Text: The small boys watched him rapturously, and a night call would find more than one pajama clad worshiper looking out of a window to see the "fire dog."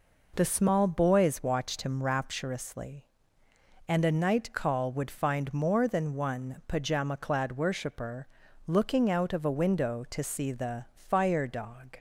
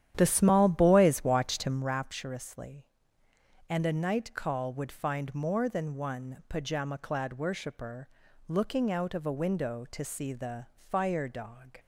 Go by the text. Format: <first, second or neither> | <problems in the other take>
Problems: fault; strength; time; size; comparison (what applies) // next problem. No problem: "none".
first | starts louder than the rest; strong; until 2.0 s; 10.5 dB // pauses between "worshiper" and "looking"; at 8.0 s; 0.40 s long; also in the first